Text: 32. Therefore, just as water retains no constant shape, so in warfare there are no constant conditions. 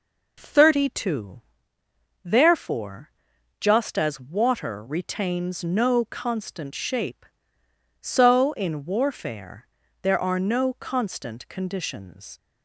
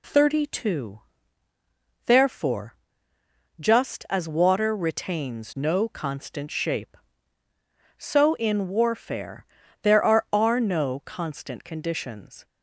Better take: first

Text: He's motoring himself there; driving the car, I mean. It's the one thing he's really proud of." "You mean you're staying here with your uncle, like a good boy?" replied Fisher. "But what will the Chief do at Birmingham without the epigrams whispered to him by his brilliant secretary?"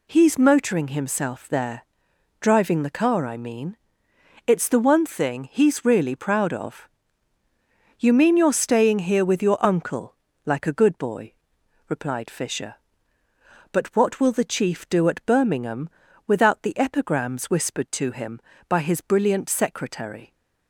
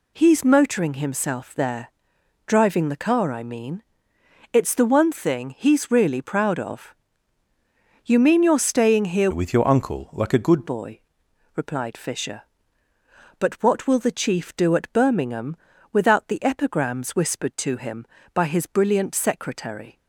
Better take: first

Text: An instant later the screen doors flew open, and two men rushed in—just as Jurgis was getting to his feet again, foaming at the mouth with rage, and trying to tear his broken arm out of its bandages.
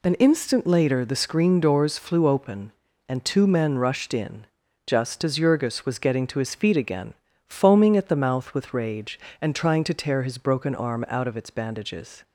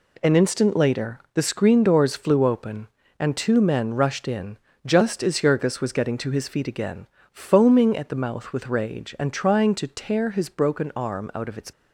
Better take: first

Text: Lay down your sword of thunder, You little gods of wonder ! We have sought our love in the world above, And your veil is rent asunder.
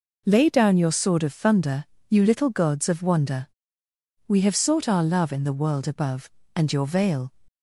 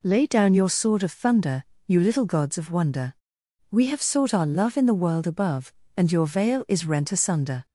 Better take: second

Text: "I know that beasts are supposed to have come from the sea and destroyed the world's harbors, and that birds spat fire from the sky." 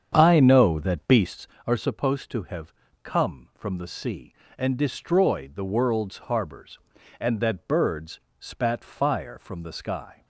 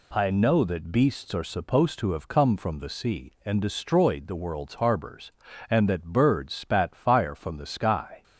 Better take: second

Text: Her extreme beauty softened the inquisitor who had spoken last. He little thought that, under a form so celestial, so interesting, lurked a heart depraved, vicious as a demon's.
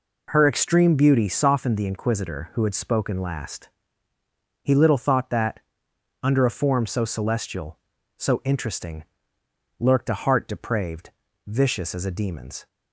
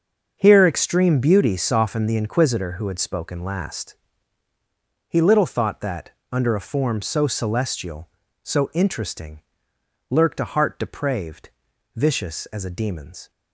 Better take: first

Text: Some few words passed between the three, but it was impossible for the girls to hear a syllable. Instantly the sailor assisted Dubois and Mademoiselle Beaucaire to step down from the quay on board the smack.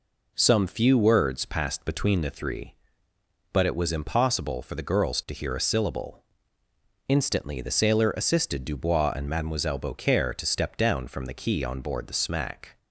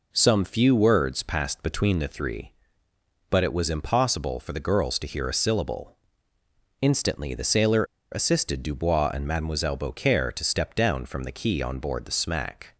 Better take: first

